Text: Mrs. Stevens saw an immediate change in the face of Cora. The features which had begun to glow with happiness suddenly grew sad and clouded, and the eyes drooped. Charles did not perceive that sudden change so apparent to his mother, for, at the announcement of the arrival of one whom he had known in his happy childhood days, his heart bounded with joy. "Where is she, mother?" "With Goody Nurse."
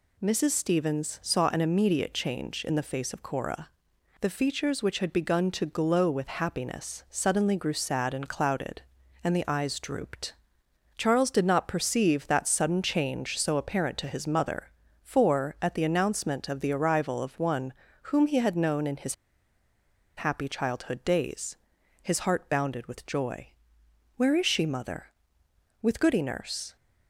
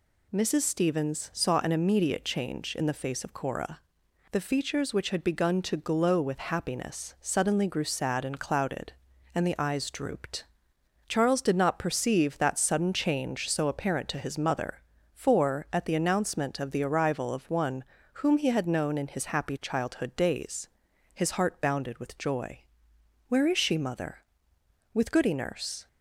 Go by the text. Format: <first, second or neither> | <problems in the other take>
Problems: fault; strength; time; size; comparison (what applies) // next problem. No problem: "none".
second | pauses between "one" and "whom"; slight; at 17.7 s; 0.32 s long; slight in the second // pauses between "his" and "happy"; at 19.1 s; 1.0 s long